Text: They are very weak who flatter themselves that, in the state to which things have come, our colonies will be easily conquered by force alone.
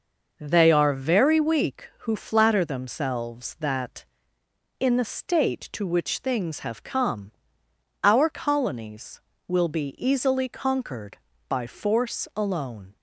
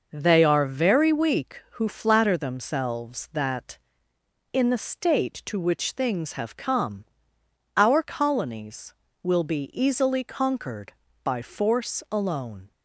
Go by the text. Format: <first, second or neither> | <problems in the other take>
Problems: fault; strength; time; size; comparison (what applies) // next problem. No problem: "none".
neither | none